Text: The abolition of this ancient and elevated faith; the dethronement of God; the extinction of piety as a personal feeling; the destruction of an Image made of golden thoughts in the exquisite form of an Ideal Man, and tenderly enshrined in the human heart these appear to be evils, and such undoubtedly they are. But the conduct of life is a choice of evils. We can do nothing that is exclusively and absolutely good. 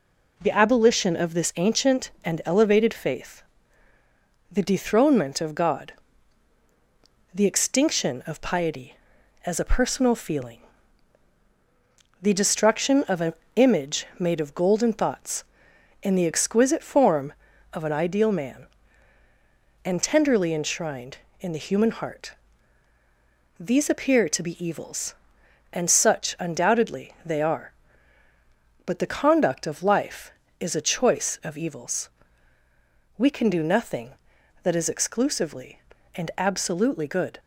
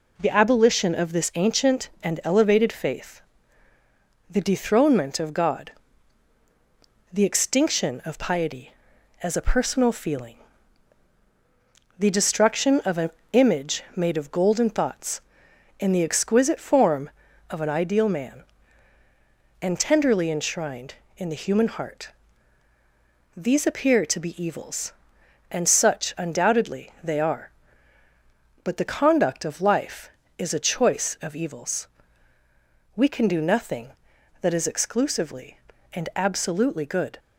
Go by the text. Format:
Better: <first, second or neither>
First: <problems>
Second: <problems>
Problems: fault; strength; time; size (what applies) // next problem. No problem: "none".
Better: neither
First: pauses between "an" and "Image"; slight; at 13.3 s; 0.22 s long // pauses between "heart" and "these"; strong; at 22.3 s; 1.2 s long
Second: pauses between "an" and "Image"; slight; at 13.0 s; 0.22 s long // pauses between "heart" and "these"; strong; at 22.0 s; 1.2 s long